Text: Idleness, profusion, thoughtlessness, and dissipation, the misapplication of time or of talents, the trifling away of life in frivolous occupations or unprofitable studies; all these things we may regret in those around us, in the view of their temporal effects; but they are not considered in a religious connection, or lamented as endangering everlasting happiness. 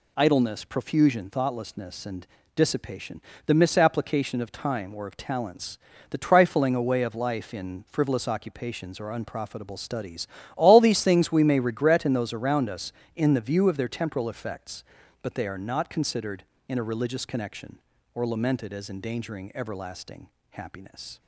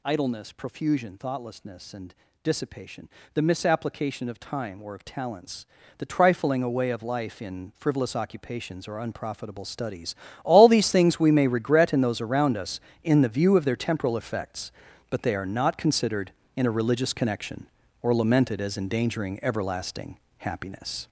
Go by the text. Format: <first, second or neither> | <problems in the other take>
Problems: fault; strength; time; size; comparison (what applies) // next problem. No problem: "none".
first | gets louder; throughout; 7 dB // pauses between "and" and "dissipation"; slight; at 2.1 s; 0.28 s long; slight in the first // pauses between "everlasting" and "happiness"; slight; at 20.1 s; 0.24 s long; slight in the first